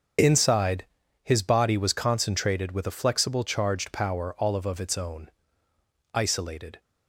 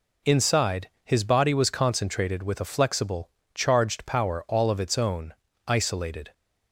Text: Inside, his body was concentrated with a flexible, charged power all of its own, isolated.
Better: second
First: starts louder than the rest; until 1.6 s; 6.5 dB // says "of" twice; at 4.6 s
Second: none

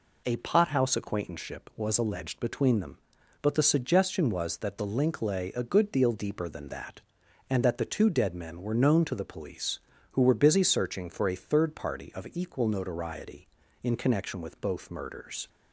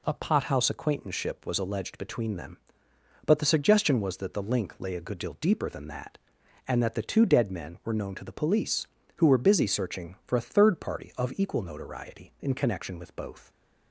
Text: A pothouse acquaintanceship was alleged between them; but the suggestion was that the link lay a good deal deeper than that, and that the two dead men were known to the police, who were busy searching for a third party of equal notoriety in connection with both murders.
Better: first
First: none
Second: stops before "murders"; at 13.5 s

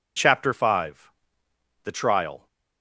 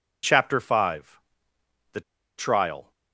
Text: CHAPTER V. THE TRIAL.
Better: first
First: none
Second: pauses between "THE" and "TRIAL"; at 2.0 s; 0.37 s long

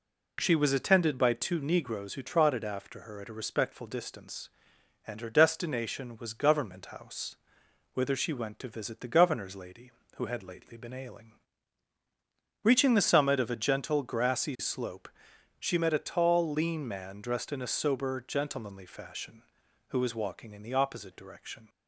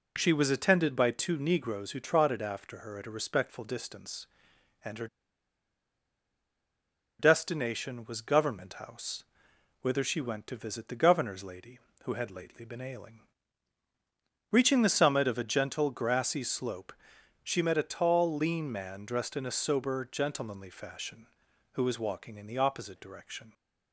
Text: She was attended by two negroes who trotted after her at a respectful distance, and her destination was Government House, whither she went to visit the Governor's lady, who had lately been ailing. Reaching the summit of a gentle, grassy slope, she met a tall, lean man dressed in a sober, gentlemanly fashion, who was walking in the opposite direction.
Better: first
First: none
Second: pauses between "her" and "destination"; strong; at 5.0 s; 2.1 s long

